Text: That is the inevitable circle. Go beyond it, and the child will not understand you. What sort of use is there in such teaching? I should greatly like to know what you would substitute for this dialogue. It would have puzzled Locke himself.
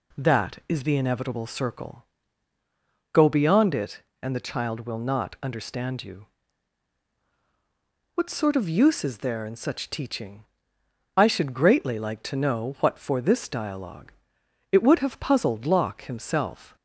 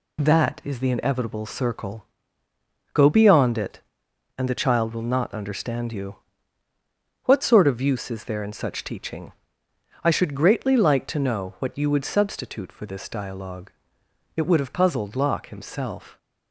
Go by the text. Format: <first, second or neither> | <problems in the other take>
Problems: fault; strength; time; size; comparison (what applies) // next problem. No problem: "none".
second | skips "you would substitute"; at 12.9 s